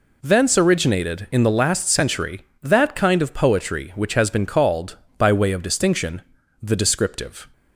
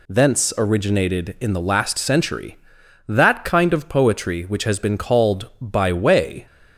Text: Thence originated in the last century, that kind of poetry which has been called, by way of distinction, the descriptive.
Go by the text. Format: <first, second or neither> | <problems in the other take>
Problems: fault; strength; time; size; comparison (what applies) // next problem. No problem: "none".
first | stops before "of distinction the descriptive"; at 6.4 s